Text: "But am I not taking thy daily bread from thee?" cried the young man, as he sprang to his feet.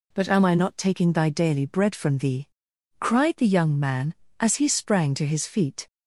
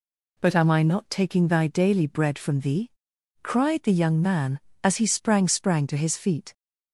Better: first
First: none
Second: says "sprang" twice; at 5.4 s

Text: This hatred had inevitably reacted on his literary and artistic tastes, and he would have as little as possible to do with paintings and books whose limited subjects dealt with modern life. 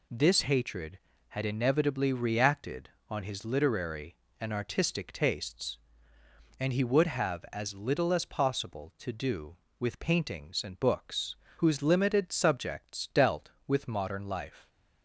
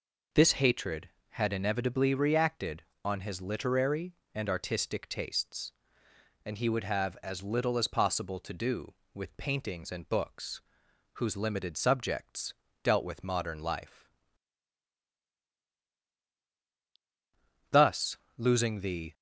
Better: first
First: pauses between "books" and "whose"; slight; at 11.3 s; 0.24 s long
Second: pauses between "books" and "whose"; noticeable; at 10.6 s; 0.54 s long // pauses between "subjects" and "dealt"; slight; at 12.5 s; 0.28 s long // goes on to say "Thus losing the"; from 17.7 s on; 1.4 s long

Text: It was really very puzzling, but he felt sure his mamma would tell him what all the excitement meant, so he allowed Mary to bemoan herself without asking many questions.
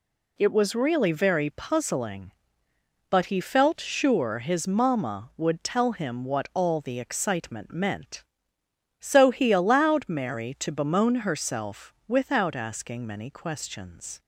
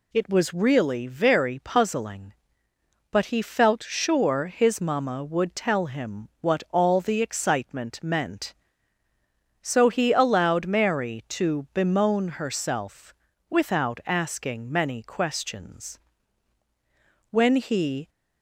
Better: first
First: none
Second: pauses between "herself" and "without"; slight; at 13.1 s; 0.36 s long // goes on to say "When he"; noticeable; from 17.3 s on; 0.78 s long

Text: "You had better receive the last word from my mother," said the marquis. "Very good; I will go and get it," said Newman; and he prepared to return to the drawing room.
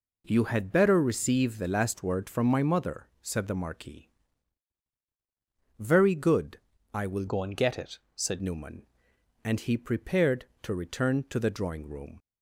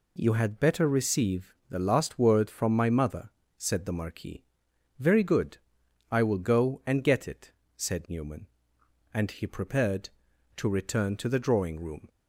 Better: second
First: changes voice from "go" to "said"; from 7.2 to 8.4 s; 1.2 s long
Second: none

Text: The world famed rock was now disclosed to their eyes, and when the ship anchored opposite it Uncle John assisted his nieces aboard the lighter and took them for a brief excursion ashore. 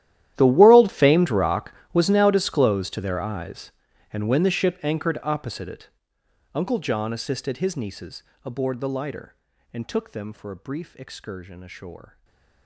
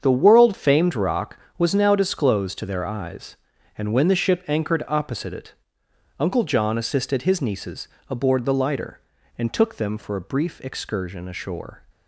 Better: second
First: gets quieter; strong; throughout; 21.5 dB // starts louder than the rest; strong; until 1.3 s; 12.5 dB // pauses between "it" and "Uncle"; noticeable; at 5.8 s; 0.66 s long // pauses between "nieces" and "aboard"; slight; at 8.2 s; 0.22 s long // stays silent after the last word; slight; from 12.0 s on; 0.6 s long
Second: starts louder than the rest; strong; until 1.0 s; 7.5 dB // pauses between "it" and "Uncle"; noticeable; at 5.5 s; 0.66 s long // pauses between "nieces" and "aboard"; slight; at 7.8 s; 0.22 s long

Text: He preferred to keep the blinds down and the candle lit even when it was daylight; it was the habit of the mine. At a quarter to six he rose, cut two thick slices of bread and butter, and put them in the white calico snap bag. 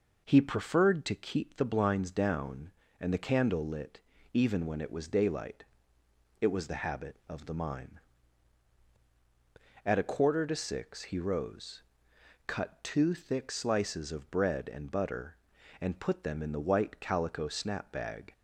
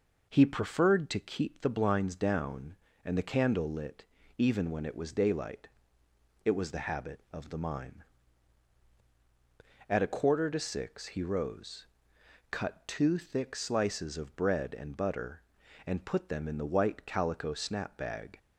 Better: neither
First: pauses between "lit" and "even"; slight; at 3.9 s; 0.32 s long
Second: pauses between "lit" and "even"; slight; at 4.0 s; 0.32 s long

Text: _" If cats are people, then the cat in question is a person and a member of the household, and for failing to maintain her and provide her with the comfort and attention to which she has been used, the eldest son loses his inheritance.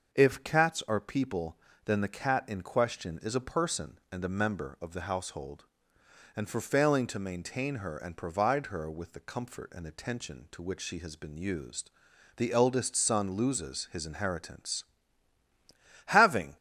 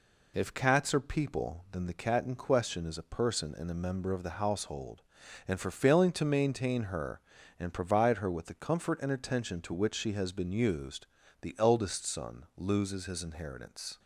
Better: second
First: starts louder than the rest; noticeable; until 1.1 s; 6 dB // goes on to say "Having"; from 16.0 s on; 0.52 s long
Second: none

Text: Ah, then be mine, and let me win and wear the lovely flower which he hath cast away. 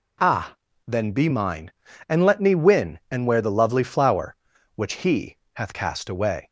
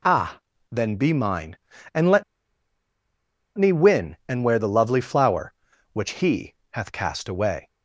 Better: first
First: pauses between "he" and "hath"; slight; at 5.3 s; 0.16 s long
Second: pauses between "let" and "me"; strong; at 2.2 s; 1.3 s long // pauses between "he" and "hath"; slight; at 6.5 s; 0.16 s long

